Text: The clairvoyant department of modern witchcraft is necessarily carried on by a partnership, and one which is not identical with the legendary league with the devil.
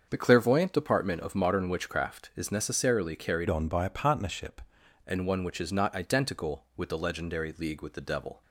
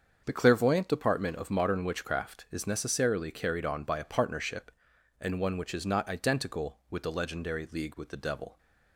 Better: second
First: starts louder than the rest; until 1.1 s; 7 dB // changes voice from "on" to "partnership"; from 3.4 to 4.6 s; 1.2 s long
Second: starts louder than the rest; until 1.2 s; 7 dB

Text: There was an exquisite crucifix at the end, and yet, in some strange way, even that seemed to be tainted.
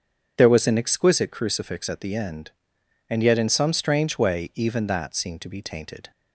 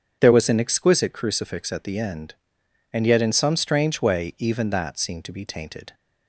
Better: neither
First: starts louder than the rest; strong; until 1.3 s; 7.5 dB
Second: starts louder than the rest; strong; until 1.2 s; 7.5 dB

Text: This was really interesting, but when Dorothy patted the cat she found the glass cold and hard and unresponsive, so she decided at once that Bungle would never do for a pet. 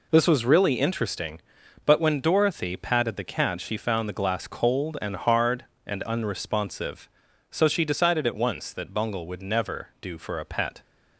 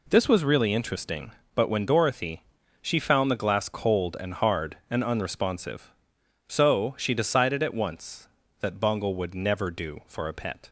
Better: first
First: none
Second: skips "patted the cat"; at 2.6 s

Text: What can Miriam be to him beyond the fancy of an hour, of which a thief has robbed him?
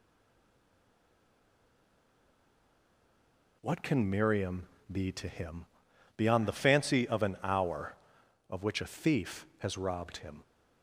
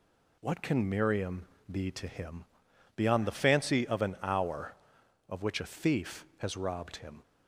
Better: second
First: stays silent before the first word; strong; until 3.6 s; 3.6 s long // pauses between "Miriam" and "be"; slight; at 4.6 s; 0.22 s long // pauses between "him" and "beyond"; noticeable; at 5.6 s; 0.50 s long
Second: pauses between "Miriam" and "be"; slight; at 1.4 s; 0.22 s long // pauses between "him" and "beyond"; noticeable; at 2.4 s; 0.50 s long

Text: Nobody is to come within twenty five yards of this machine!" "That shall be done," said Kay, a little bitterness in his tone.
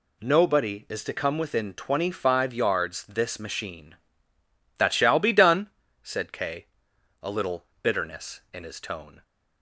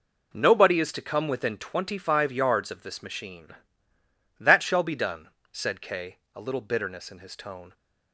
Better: second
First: skips "of"; at 3.0 s // pauses between "little" and "bitterness"; slight; at 7.6 s; 0.18 s long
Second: none

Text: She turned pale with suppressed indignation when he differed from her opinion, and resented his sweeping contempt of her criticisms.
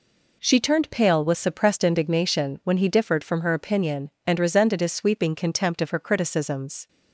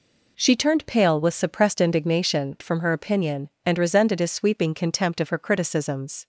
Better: first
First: none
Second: skips "when he differed"; at 2.5 s

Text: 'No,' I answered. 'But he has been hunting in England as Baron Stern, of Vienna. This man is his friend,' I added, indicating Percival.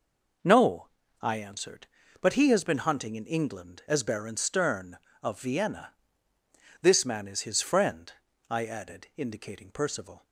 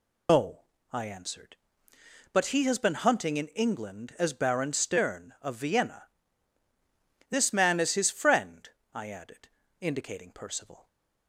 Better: first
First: none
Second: loses the start of "No"; at 0.2 s; 140 ms

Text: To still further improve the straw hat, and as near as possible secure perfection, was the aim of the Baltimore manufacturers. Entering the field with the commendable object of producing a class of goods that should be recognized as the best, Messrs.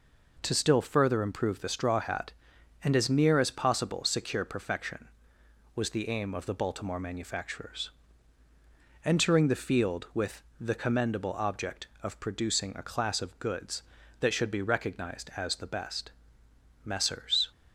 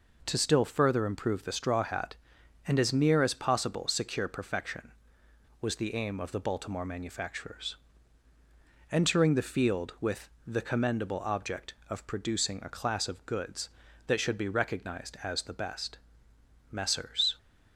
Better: neither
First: pauses between "with" and "the"; slight; at 10.4 s; 0.16 s long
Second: pauses between "with" and "the"; slight; at 10.2 s; 0.16 s long

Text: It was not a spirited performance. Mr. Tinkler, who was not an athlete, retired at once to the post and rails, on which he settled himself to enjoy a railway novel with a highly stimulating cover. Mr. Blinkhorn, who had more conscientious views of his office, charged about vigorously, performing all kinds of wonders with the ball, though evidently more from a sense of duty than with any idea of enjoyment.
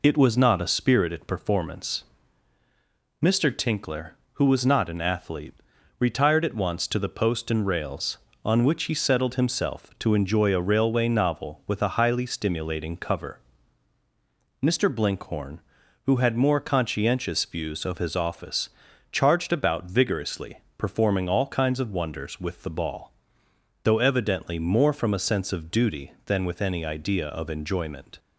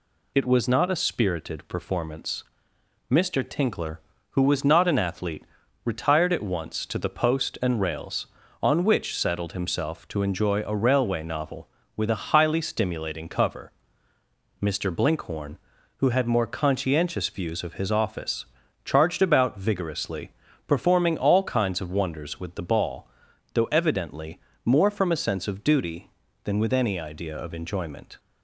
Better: first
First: none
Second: skips "he"; at 9.1 s // pauses between "evidently" and "more"; slight; at 24.3 s; 0.24 s long

